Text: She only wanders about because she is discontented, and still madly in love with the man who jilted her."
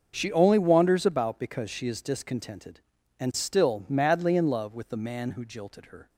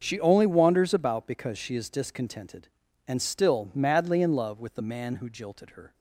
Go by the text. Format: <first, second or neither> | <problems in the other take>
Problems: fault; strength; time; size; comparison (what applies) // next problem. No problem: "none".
neither | starts louder than the rest; the same in both